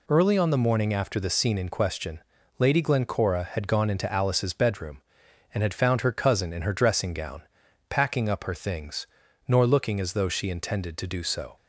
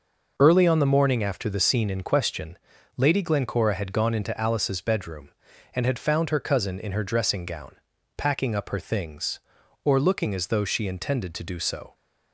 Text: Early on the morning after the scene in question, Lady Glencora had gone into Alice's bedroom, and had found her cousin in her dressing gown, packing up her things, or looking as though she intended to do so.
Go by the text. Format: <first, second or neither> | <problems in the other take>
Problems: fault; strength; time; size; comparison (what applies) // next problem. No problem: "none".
second | says "nor" for "or"; at 9.4 s